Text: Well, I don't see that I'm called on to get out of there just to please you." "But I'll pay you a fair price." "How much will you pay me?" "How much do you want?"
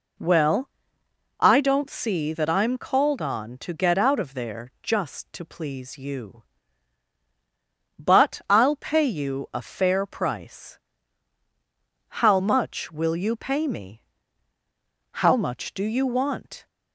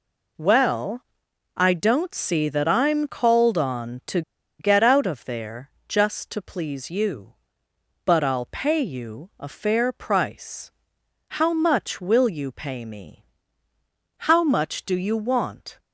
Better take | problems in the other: first | pauses between "to" and "get"; at 4.2 s; 0.38 s long // pauses between "there" and "just"; slight; at 5.7 s; 0.18 s long

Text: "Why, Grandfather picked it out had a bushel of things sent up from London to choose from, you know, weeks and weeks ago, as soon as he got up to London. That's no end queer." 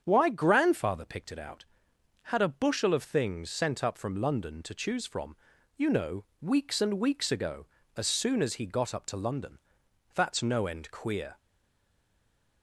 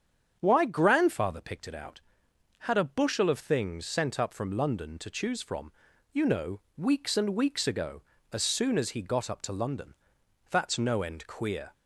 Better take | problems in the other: second | starts louder than the rest; strong; until 1.0 s; 8 dB; strong in the second // stays silent after the last word; noticeable; from 11.3 s on; 1.3 s long

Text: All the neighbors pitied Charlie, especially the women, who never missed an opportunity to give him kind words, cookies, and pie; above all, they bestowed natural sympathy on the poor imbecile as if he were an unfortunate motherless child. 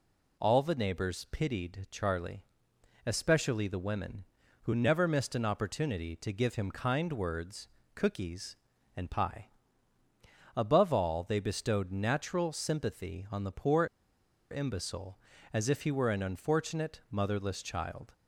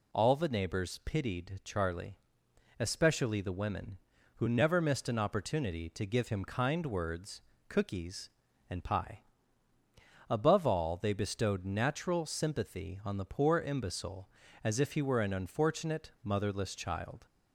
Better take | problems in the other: second | pauses between "poor" and "imbecile"; noticeable; at 13.8 s; 0.65 s long

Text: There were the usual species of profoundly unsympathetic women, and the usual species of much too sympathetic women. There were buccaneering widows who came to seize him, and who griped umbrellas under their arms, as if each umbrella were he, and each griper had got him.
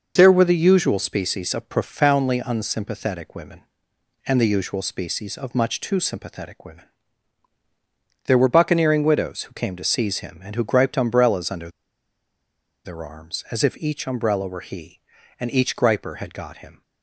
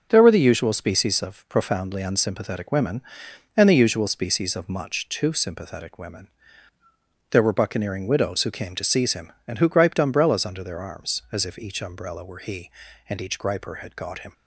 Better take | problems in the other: second | pauses between "under" and "their"; at 11.6 s; 1.1 s long

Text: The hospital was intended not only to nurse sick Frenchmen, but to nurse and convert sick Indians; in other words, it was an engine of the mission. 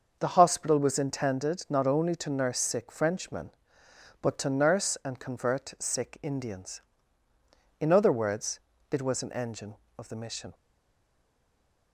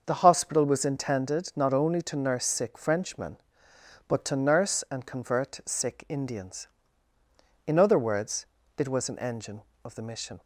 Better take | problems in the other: second | starts louder than the rest; until 1.2 s; 6.5 dB; also in the second // stays silent after the last word; noticeable; from 10.5 s on; 1.4 s long

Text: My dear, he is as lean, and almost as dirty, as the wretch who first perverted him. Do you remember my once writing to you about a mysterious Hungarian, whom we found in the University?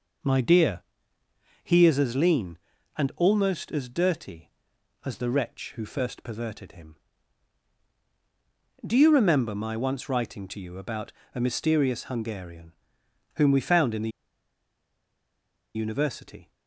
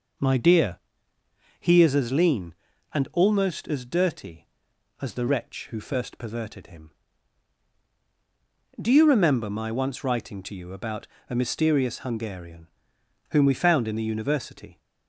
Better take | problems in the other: second | pauses between "about" and "a"; slight; at 11.1 s; 0.22 s long; slight in the second // pauses between "the" and "University"; strong; at 14.1 s; 1.6 s long

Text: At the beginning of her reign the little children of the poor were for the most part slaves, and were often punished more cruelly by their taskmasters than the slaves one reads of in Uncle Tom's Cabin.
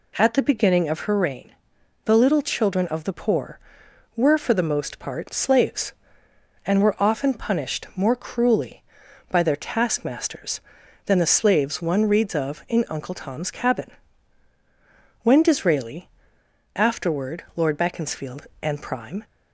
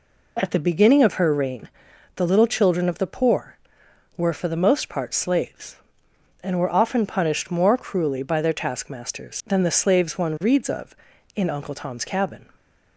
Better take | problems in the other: second | pauses between "reign" and "the"; noticeable; at 1.5 s; 0.50 s long; noticeable in the second // goes on to say "When Disraeli afterward Lord Beaconsfield and Prime"; strong; from 15.2 s on; 4.0 s long

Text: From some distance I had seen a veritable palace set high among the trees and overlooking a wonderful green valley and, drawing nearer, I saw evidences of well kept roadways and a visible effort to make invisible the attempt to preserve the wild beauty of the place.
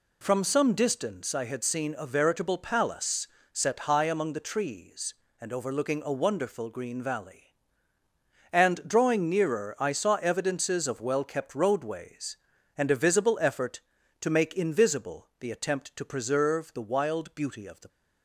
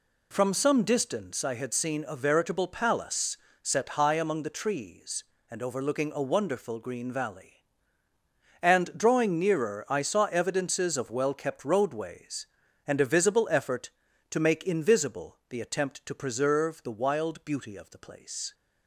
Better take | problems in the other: second | pauses between "palace" and "set"; slight; at 3.2 s; 0.26 s long; slight in the second // stops before "place"; at 17.8 s

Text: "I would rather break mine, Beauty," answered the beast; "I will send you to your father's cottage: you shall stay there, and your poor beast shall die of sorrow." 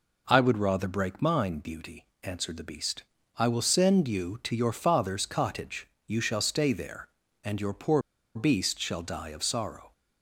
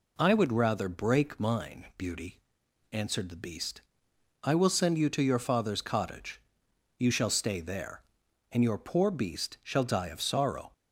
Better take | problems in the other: second | pauses between "poor" and "beast"; slight; at 8.0 s; 0.34 s long

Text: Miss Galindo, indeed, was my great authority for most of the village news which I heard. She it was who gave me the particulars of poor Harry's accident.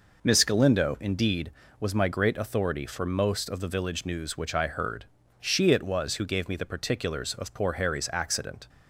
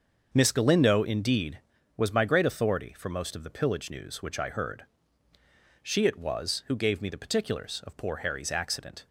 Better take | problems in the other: first | starts louder than the rest; until 1.3 s; 6.5 dB // says "pillage" for "village"; at 3.4 s

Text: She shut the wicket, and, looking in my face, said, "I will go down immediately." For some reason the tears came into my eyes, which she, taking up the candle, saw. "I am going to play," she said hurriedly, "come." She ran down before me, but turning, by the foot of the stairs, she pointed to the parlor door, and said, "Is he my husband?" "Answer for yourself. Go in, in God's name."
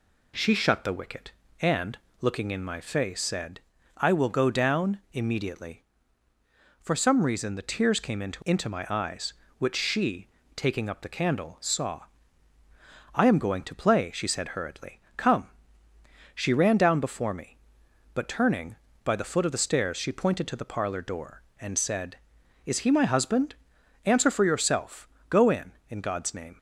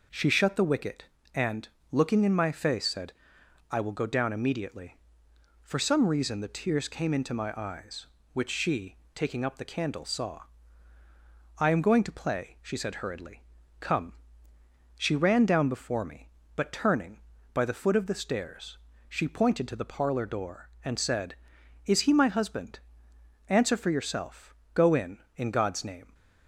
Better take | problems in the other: second | says "into" twice; at 8.4 s

